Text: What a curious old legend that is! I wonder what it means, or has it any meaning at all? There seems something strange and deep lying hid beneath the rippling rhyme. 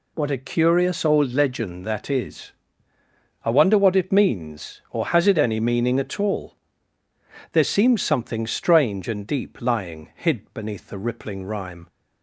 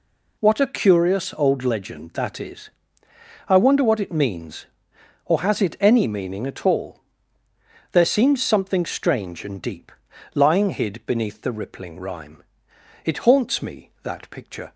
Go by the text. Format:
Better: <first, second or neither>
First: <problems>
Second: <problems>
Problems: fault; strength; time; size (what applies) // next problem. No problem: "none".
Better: first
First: none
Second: pauses between "deep" and "lying"; at 9.9 s; 0.44 s long // goes on to say "It haunts me that picture"; strong; from 13.0 s on; 1.7 s long